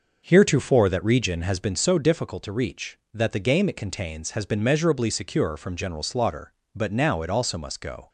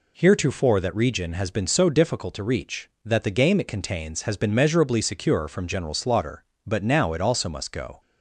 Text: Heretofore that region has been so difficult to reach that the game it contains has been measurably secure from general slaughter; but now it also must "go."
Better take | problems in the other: second | starts louder than the rest; noticeable; until 1.7 s; 6 dB

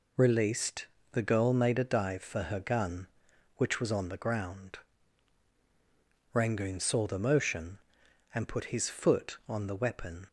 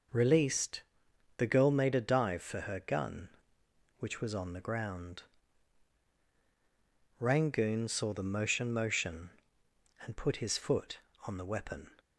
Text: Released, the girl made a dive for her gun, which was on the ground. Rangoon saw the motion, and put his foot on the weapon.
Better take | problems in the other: first | says "motion" twice; at 8.7 s

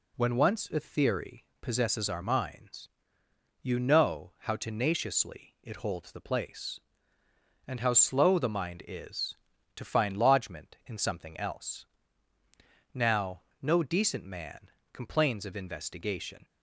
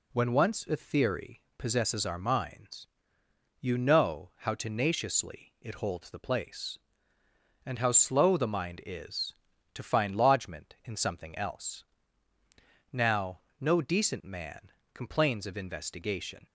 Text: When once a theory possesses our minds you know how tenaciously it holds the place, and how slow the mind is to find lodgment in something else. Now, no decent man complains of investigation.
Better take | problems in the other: neither | pauses between "theory" and "possesses"; slight; the same in both // pauses between "minds" and "you"; noticeable; the same in both // pauses between "man" and "complains"; slight; the same in both

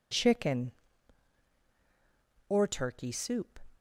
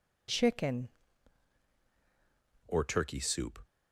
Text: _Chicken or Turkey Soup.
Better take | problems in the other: first | changes voice at "or"; from 2.6 s on; 0.9 s long

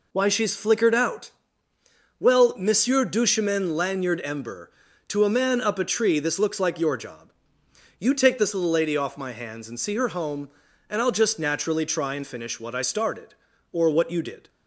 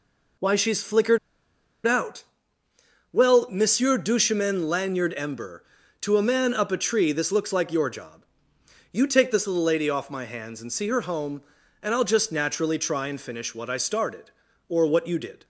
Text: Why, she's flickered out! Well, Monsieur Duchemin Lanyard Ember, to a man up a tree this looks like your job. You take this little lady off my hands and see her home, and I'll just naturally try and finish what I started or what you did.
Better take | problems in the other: first | pauses between "flickered" and "out"; noticeable; at 1.1 s; 0.68 s long

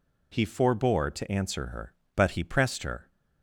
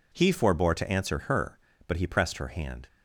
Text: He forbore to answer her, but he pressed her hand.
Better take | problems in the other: second | stops before "hand"; at 3.1 s

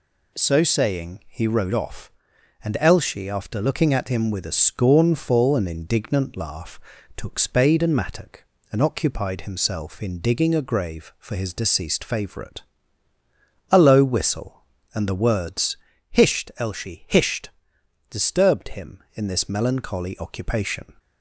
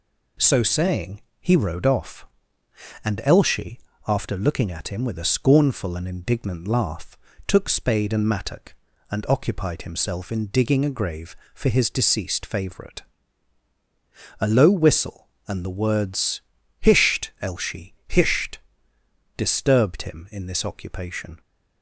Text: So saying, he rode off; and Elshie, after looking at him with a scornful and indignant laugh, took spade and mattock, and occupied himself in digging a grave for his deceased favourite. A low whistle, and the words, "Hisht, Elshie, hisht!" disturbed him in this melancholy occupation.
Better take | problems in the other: first | skips "melancholy"; at 20.6 s

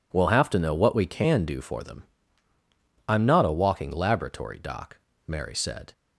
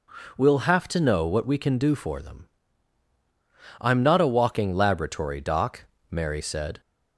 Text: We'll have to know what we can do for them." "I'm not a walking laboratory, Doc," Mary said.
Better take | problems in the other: neither | none

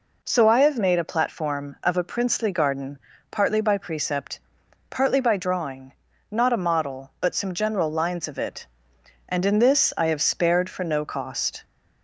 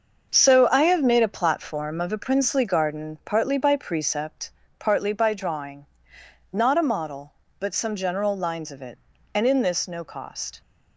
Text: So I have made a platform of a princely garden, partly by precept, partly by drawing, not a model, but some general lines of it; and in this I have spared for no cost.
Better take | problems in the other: first | starts louder than the rest; until 1.3 s; 6.5 dB // skips "I have spared for"; at 9.8 s

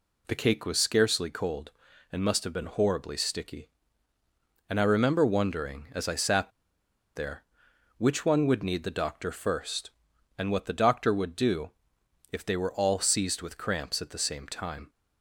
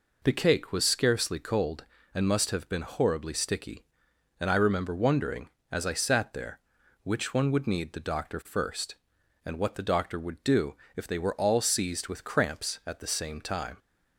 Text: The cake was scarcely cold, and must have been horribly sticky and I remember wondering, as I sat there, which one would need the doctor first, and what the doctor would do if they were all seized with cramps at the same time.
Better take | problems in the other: second | pauses between "sat" and "there"; noticeable; at 6.5 s; 0.64 s long // pauses between "do" and "if"; noticeable; at 11.6 s; 0.62 s long; slight in the second

